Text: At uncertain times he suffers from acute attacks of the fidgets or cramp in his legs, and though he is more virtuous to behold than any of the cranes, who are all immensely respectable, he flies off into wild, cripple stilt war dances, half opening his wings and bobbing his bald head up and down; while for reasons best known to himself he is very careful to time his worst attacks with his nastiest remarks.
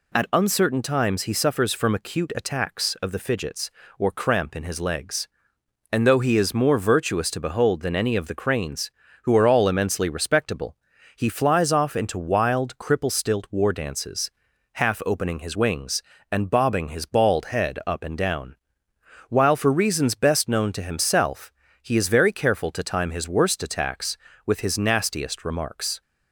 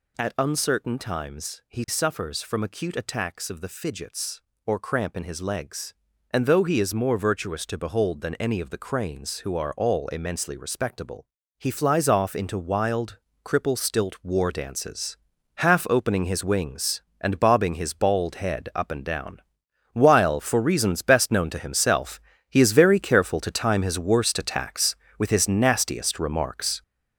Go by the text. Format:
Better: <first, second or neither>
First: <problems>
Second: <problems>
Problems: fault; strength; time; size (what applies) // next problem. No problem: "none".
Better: first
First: pauses between "himself" and "he"; slight; at 21.5 s; 0.28 s long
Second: gets louder; throughout; 7 dB // pauses between "himself" and "he"; slight; at 22.1 s; 0.32 s long